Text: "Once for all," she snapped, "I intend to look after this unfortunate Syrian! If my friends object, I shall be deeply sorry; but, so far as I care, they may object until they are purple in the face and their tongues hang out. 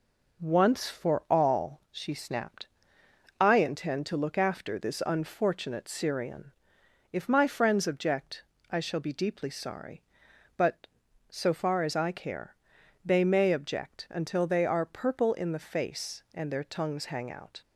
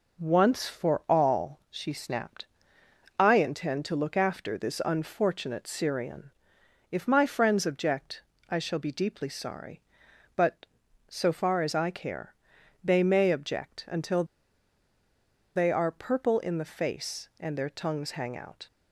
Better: first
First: none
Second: pauses between "until" and "they"; strong; at 14.2 s; 1.3 s long

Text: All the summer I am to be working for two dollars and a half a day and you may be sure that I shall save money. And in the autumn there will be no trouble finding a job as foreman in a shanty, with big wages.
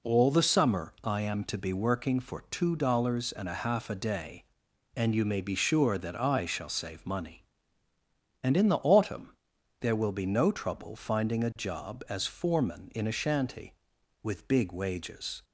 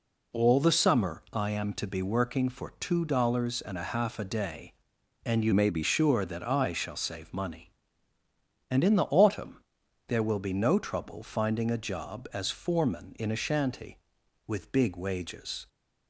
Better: first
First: pauses between "autumn" and "there"; noticeable; at 9.3 s; 0.46 s long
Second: changes voice from "may" to "be"; from 5.5 to 5.8 s; 0.3 s long // pauses between "autumn" and "there"; noticeable; at 9.6 s; 0.46 s long

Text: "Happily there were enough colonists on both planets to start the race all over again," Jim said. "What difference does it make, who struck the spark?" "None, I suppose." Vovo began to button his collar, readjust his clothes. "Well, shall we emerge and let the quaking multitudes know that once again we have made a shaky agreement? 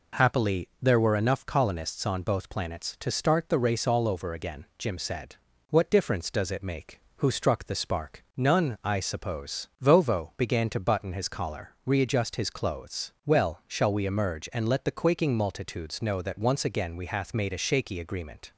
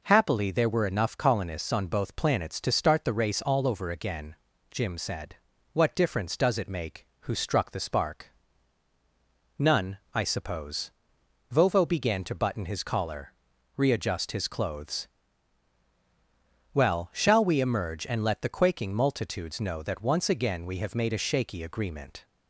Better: second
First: says "hath" for "have"; at 17.0 s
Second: none

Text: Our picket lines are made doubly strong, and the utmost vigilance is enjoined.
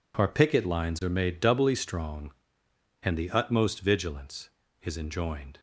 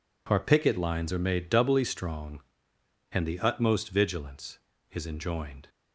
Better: neither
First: none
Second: none

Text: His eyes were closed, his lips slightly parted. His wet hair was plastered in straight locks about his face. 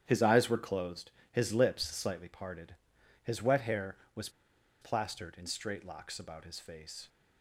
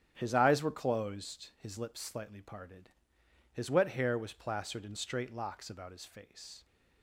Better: second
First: starts louder than the rest; strong; until 1.0 s; 10 dB // pauses between "was" and "plastered"; noticeable; at 4.2 s; 0.52 s long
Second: starts louder than the rest; strong; until 1.1 s; 9.5 dB

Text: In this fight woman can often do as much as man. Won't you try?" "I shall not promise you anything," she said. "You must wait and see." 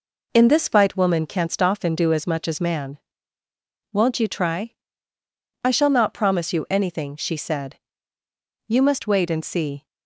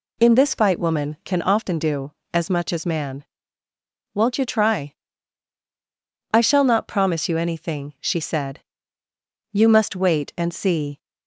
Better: second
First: says "canst" for "can"; at 1.2 s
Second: none

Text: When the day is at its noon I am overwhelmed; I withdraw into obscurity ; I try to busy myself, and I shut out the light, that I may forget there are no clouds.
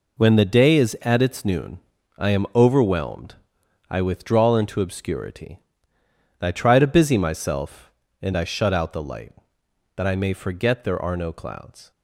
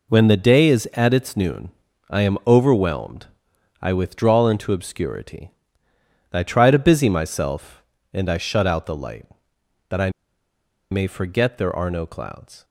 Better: first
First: pauses between "noon" and "I"; at 1.7 s; 0.40 s long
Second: pauses between "noon" and "I"; at 1.6 s; 0.40 s long // pauses between "I" and "may"; noticeable; at 10.0 s; 0.82 s long

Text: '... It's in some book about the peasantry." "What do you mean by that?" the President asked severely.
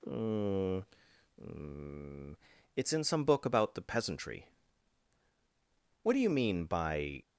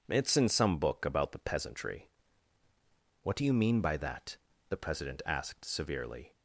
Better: second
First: stops before "that the President asked severely"; at 7.2 s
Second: none

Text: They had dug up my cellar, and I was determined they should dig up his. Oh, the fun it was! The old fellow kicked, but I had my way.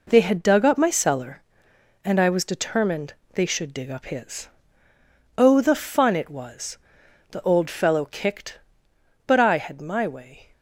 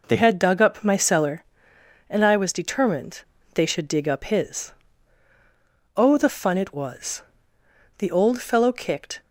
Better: first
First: pauses between "determined" and "they"; slight; at 3.1 s; 0.22 s long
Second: pauses between "determined" and "they"; slight; at 3.2 s; 0.32 s long // stops before "but I had my way"; at 9.2 s

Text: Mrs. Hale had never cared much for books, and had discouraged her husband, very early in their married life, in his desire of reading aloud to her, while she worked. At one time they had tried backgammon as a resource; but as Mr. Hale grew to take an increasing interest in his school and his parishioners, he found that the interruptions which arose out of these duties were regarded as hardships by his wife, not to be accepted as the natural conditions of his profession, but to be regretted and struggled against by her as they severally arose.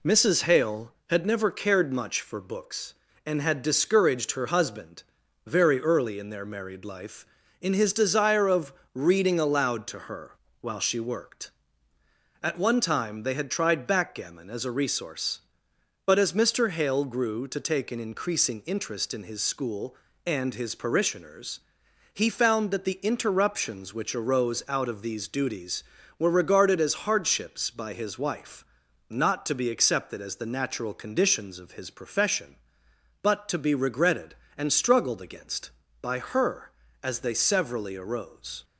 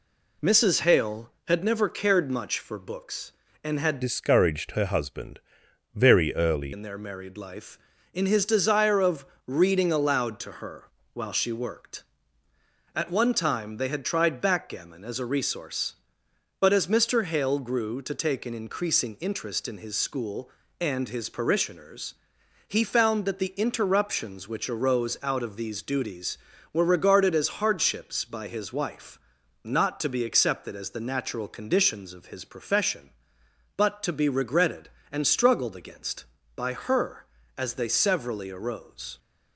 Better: first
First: pauses between "of" and "reading"; slight; at 8.7 s; 0.22 s long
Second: changes voice from "discouraged" to "early"; from 4.0 to 6.7 s; 2.7 s long // pauses between "of" and "reading"; slight; at 9.2 s; 0.22 s long

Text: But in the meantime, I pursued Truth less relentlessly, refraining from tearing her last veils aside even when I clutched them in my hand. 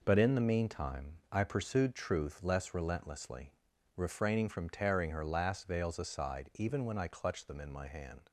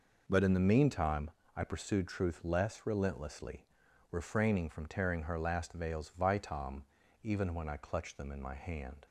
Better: first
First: none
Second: says "vitam" for "aside"; at 6.1 s

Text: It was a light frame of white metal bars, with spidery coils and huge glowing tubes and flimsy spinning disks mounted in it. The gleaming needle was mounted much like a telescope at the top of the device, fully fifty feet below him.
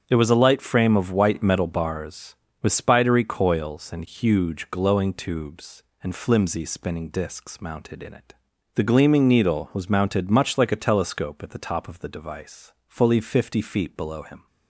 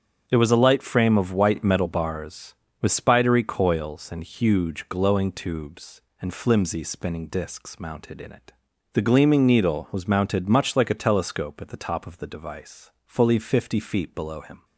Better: neither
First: starts louder than the rest; strong; until 1.0 s; 8 dB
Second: starts louder than the rest; strong; until 1.2 s; 8 dB

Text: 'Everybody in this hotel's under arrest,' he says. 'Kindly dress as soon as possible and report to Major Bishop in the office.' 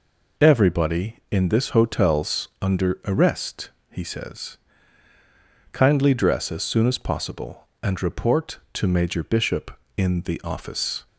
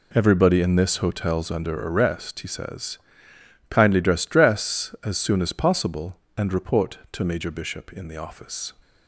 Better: first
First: none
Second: says "dress" twice; at 4.2 s

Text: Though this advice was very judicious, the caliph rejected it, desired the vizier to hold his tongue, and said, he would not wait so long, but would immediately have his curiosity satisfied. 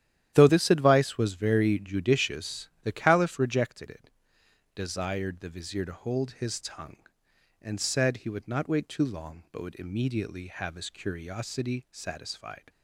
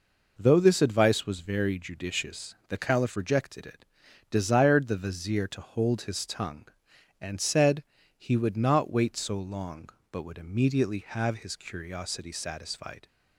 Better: second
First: starts louder than the rest; strong; until 1.3 s; 11 dB // says "too" for "so"; at 8.8 s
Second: none

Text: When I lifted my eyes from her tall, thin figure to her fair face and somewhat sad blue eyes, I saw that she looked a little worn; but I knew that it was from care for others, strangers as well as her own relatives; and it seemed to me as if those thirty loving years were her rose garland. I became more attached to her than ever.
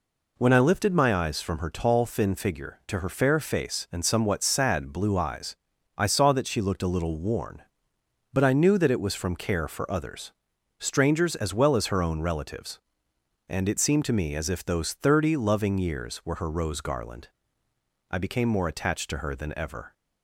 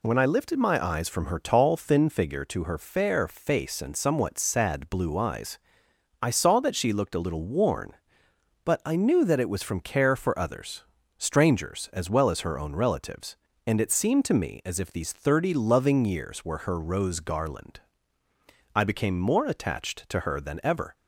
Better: first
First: none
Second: says "these" for "those"; at 14.9 s

